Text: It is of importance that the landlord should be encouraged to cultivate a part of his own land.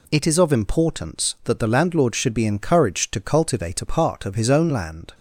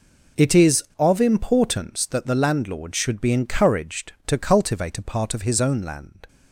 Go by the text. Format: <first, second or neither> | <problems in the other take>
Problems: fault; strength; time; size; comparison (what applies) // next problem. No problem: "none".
first | gets quieter; strong; throughout; 14.5 dB